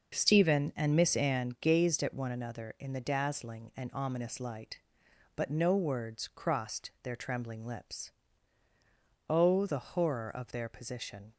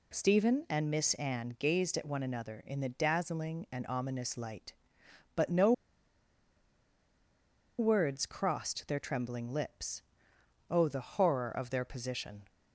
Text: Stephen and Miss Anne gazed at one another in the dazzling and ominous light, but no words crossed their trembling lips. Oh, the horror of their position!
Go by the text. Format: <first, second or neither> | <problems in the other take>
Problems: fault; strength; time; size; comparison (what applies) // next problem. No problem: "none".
first | pauses between "no" and "words"; strong; at 5.7 s; 2.0 s long